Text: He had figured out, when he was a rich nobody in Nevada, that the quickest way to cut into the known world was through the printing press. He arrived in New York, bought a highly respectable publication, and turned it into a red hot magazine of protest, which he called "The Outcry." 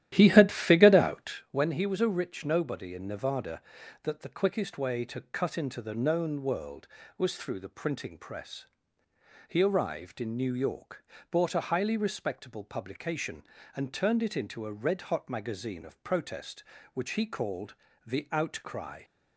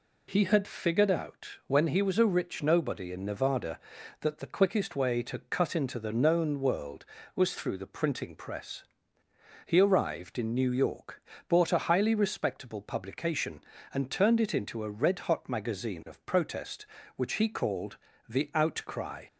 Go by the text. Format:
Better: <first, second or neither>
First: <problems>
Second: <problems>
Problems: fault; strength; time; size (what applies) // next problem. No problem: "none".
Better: second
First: starts louder than the rest; strong; until 1.5 s; 12.5 dB // pauses between "called" and "The"; slight; at 17.7 s; 0.28 s long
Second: pauses between "called" and "The"; slight; at 17.9 s; 0.28 s long